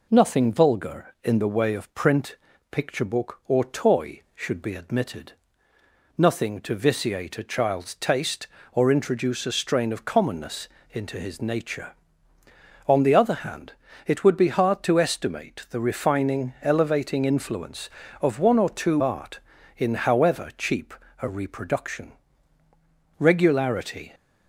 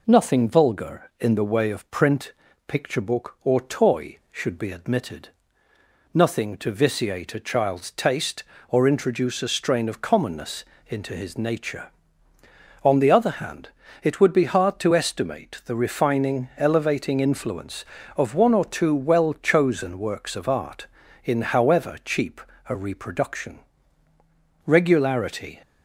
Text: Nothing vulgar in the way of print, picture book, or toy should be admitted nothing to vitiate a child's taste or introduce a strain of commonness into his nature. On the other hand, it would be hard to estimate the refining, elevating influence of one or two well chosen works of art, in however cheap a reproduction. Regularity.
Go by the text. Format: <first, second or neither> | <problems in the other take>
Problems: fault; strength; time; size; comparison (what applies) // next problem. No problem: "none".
second | pauses between "admitted" and "nothing"; noticeable; at 5.3 s; 0.86 s long; noticeable in the second // pauses between "commonness" and "into"; slight; at 10.6 s; 0.26 s long; slight in the second // skips "well chosen works of"; at 19.0 s // pauses between "cheap" and "a"; slight; at 20.9 s; 0.26 s long; slight in the second